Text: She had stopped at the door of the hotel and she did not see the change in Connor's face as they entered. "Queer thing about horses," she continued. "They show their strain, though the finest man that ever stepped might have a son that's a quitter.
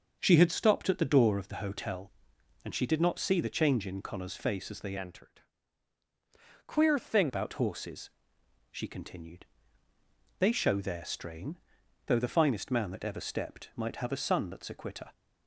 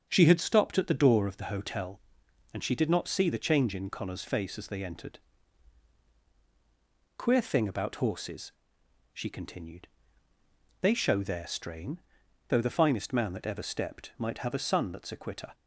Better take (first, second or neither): second